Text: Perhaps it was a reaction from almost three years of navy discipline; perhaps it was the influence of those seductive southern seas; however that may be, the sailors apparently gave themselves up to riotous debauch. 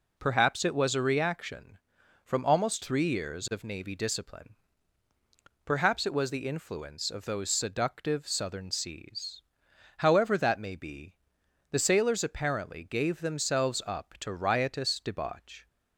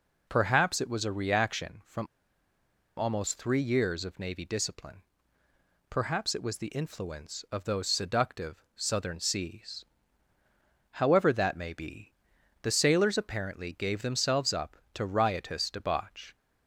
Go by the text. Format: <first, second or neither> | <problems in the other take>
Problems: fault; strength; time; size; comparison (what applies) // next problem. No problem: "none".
first | pauses between "from" and "almost"; noticeable; at 2.0 s; 0.92 s long